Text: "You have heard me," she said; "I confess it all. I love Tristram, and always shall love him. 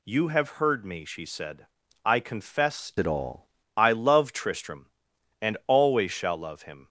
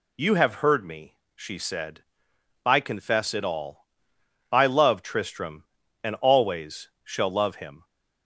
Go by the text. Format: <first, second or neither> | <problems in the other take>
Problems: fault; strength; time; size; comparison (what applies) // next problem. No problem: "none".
second | changes voice from "it" to "all"; from 2.9 to 3.4 s; 0.5 s long